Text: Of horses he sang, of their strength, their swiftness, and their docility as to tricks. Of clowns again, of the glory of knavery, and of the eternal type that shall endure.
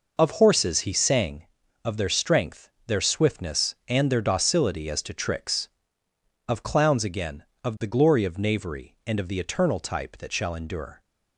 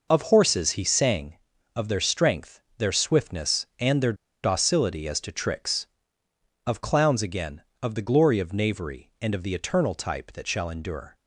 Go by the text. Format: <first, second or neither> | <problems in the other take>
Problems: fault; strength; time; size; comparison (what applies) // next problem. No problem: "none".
first | pauses between "their" and "docility"; slight; at 4.1 s; 0.29 s long